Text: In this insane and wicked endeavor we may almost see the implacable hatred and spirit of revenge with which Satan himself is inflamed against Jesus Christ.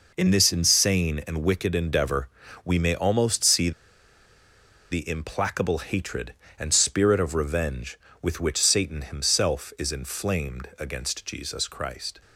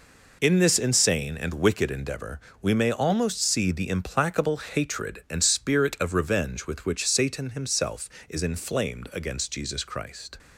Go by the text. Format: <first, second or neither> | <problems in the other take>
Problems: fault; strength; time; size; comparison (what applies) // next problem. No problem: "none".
second | pauses between "endeavor" and "we"; slight; at 2.2 s; 0.36 s long; slight in the second // pauses between "see" and "the"; at 3.7 s; 1.2 s long